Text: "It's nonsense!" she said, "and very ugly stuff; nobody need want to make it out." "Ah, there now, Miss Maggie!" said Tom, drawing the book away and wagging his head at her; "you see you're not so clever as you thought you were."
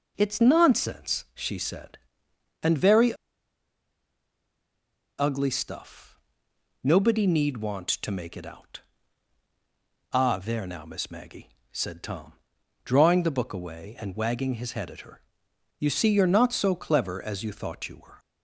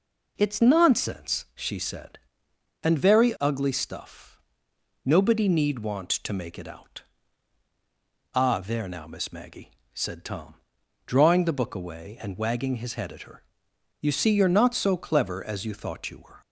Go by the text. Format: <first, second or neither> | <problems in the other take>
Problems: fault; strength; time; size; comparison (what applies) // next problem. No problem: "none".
second | pauses between "very" and "ugly"; strong; at 3.1 s; 2.0 s long